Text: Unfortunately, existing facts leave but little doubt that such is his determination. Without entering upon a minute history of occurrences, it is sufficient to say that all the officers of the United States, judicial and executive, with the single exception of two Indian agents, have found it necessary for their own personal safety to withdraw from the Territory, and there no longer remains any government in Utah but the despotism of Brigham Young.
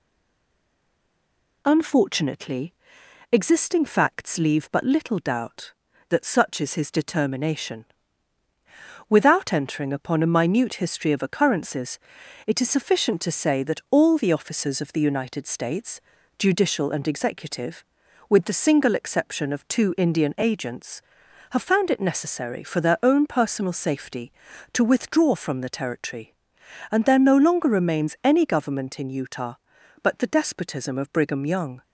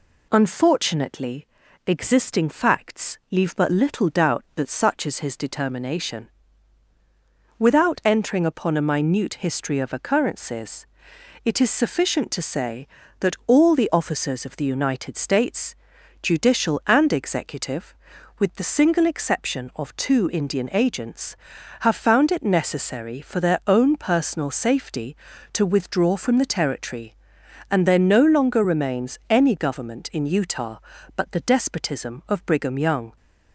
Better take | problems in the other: second | stays silent before the first word; noticeable; until 1.6 s; 1.6 s long

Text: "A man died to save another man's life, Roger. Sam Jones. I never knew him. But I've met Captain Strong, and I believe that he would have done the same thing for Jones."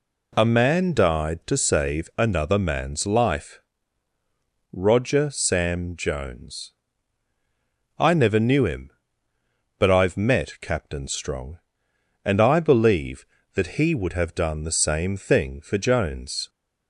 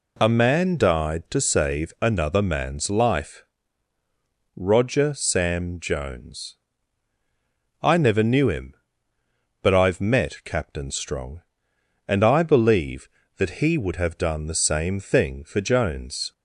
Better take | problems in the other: neither | none

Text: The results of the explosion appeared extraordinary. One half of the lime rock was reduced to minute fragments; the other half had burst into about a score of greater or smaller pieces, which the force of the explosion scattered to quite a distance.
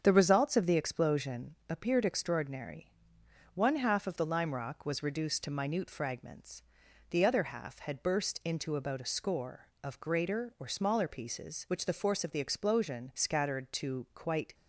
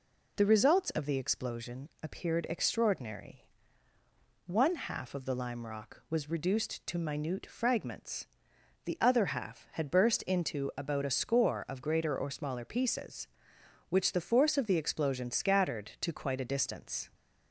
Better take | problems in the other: second | starts louder than the rest; strong; until 1.0 s; 7 dB // stops before "a distance"; at 14.5 s

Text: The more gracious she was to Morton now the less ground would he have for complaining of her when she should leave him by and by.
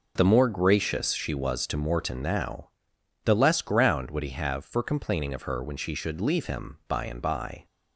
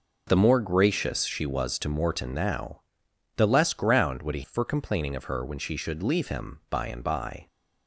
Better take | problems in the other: first | pauses between "now" and "the"; noticeable; at 2.8 s; 0.54 s long; noticeable in the first // skips "have"; at 4.4 s

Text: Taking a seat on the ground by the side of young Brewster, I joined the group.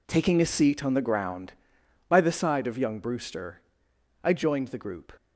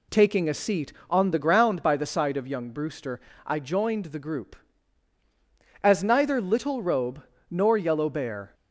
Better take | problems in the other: first | goes on to say "As neither Little Robe nor Yellow Bear"; strong; from 5.8 s on; 2.7 s long

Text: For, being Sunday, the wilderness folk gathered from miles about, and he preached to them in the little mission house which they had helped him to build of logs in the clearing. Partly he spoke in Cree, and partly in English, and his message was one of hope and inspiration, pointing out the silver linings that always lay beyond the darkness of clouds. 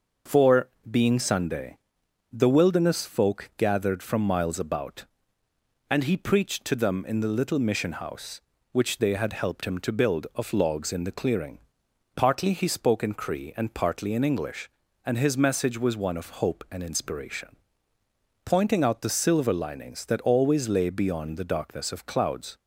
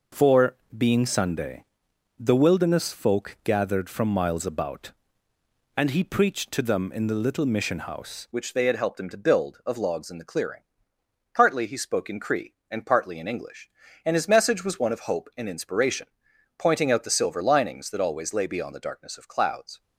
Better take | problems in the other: first | changes voice at "which"; from 8.3 s on; 11.5 s long

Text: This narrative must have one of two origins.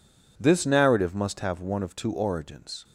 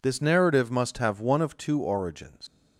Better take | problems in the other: first | leaves "origins" unfinished; at 2.4 s; 130 ms

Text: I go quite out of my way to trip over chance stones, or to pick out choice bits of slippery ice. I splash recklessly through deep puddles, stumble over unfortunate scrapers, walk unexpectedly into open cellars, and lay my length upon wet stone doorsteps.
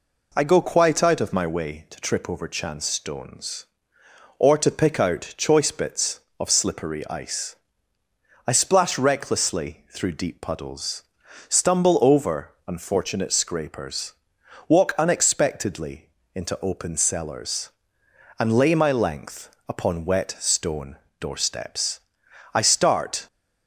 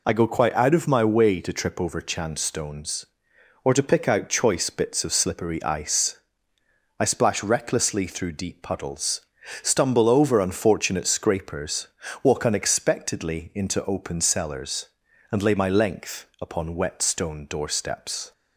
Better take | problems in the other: second | pauses between "unexpectedly" and "into"; slight; at 16.0 s; 0.26 s long // pauses between "stone" and "doorsteps"; slight; at 20.9 s; 0.24 s long // goes on to say "I start"; noticeable; from 22.5 s on; 0.72 s long

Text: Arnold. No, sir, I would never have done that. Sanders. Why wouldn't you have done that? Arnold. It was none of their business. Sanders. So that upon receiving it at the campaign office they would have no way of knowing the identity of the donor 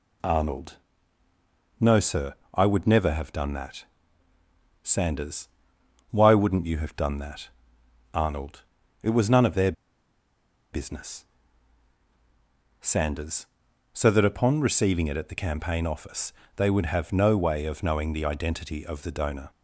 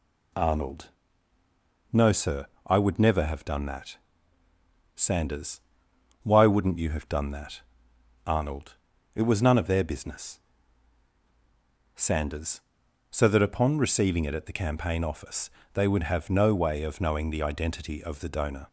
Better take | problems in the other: second | pauses between "their" and "business"; at 9.7 s; 1.0 s long // pauses between "office" and "they"; slight; at 16.3 s; 0.22 s long; slight in the second

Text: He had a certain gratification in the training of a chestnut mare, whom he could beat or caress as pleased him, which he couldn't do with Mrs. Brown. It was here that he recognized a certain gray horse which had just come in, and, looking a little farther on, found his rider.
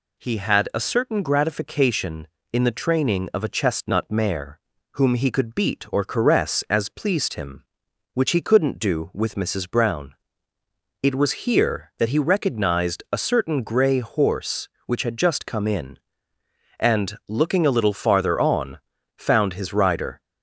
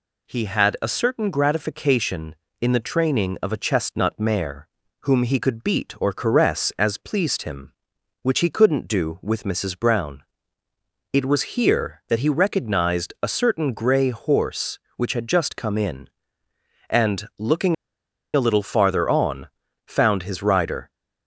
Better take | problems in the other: first | pauses between "looking" and "a"; noticeable; at 17.7 s; 0.60 s long

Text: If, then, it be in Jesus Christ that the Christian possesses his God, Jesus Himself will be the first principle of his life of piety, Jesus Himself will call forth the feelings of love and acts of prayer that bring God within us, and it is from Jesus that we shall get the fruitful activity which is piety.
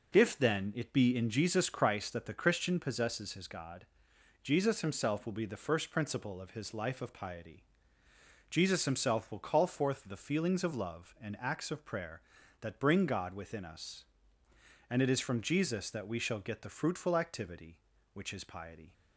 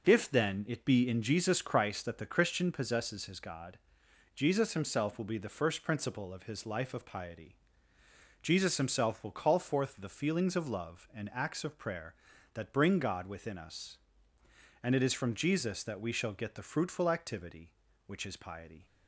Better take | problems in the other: neither | none

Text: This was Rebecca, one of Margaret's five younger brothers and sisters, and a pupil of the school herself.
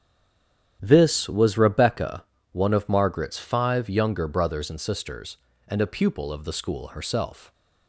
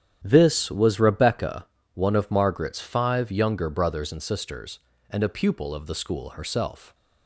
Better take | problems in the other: second | stays silent before the first word; slight; until 0.7 s; 0.7 s long // starts louder than the rest; strong; until 1.8 s; 10 dB; strong in the second

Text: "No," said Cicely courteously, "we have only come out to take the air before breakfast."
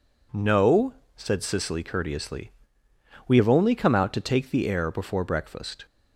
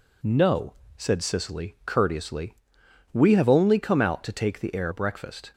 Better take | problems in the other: first | skips "before"; at 4.9 s

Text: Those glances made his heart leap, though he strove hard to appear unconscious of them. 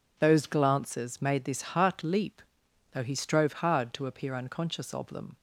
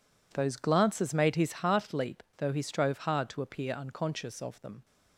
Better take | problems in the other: second | says "this" for "his"; at 1.4 s

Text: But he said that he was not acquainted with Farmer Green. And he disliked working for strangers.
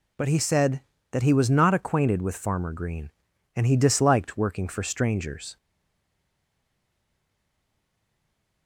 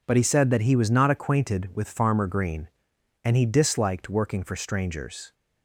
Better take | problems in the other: second | stays silent after the last word; strong; from 5.5 s on; 3.1 s long

